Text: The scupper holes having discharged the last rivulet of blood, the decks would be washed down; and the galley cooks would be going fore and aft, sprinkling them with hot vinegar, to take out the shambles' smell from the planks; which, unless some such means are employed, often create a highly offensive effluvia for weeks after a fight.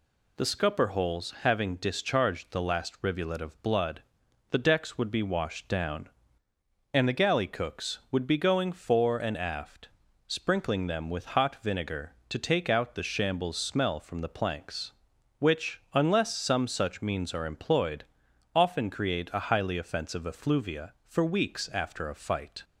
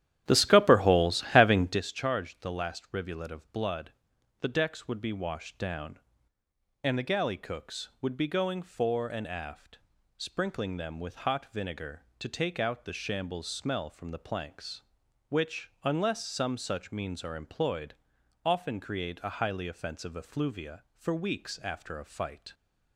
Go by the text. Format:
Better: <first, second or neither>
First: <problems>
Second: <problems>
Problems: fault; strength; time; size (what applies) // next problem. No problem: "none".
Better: first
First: none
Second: starts louder than the rest; strong; until 1.8 s; 13 dB